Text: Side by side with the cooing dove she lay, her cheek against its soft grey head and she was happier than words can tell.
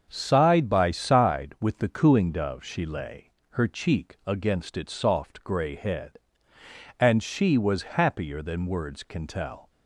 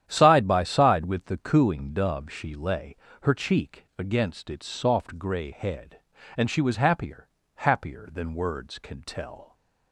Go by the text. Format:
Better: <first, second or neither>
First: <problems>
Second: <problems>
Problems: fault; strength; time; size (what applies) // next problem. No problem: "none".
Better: first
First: starts louder than the rest; until 1.1 s; 6.5 dB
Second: starts louder than the rest; strong; until 1.0 s; 10 dB // says "happier" twice; at 7.5 s